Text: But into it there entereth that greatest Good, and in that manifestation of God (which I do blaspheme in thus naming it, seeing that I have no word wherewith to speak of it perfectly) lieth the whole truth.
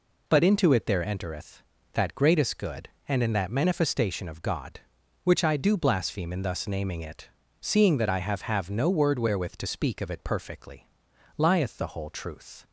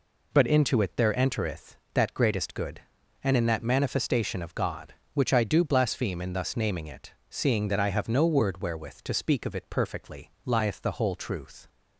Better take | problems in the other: second | says "have" twice; at 8.4 s

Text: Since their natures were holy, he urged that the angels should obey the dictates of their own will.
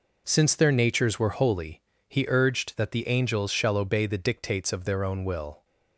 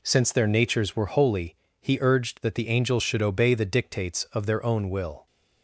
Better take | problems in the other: second | says "shall" for "should"; at 3.5 s

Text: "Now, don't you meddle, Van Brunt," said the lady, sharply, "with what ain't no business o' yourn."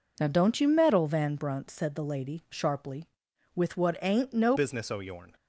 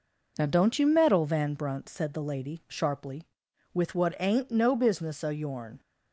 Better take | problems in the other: second | changes voice at "business"; from 4.5 s on; 0.8 s long

